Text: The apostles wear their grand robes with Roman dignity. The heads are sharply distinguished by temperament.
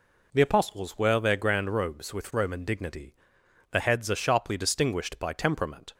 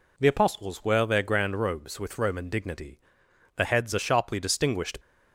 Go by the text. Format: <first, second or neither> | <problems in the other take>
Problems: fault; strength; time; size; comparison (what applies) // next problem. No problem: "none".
first | stops before "by temperament"; at 5.0 s